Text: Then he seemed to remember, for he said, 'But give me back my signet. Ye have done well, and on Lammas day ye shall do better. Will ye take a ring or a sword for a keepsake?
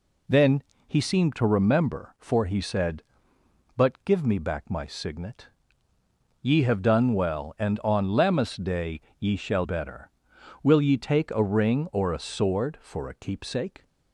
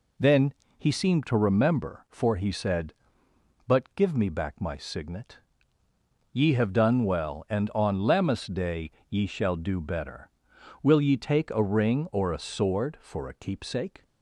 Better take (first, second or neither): second